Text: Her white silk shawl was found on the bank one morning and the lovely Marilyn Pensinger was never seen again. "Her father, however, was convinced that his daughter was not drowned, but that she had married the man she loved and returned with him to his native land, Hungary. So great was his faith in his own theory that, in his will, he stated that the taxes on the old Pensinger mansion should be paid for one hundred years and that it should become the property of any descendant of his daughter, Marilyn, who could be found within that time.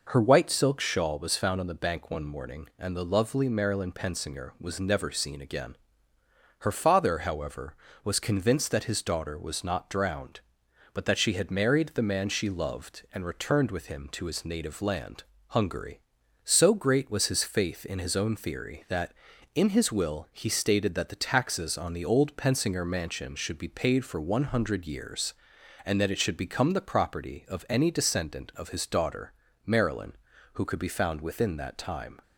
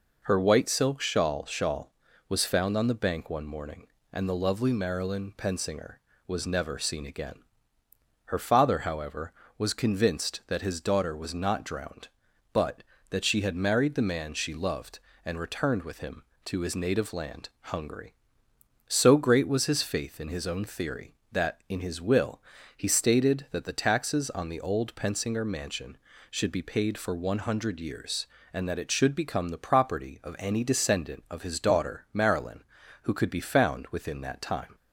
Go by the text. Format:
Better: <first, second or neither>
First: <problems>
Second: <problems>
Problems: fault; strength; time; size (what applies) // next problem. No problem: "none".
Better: first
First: none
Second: says "shawl" twice; at 1.4 s